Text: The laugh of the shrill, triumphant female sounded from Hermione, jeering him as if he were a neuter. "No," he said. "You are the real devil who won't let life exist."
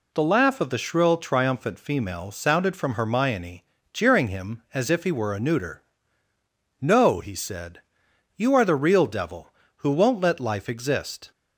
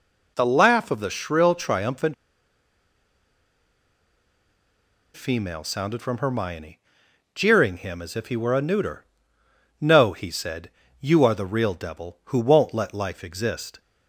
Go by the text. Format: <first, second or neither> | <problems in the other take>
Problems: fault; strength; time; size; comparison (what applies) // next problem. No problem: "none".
first | pauses between "triumphant" and "female"; strong; at 2.1 s; 3.0 s long